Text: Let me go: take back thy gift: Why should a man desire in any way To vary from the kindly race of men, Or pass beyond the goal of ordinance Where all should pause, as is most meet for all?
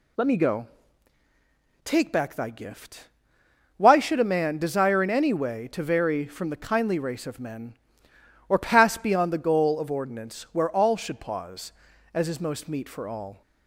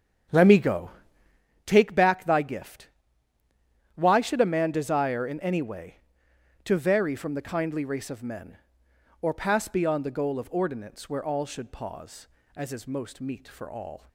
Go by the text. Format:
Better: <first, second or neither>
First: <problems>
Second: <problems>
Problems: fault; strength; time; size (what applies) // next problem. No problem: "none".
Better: first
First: none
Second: starts louder than the rest; strong; until 1.5 s; 8.5 dB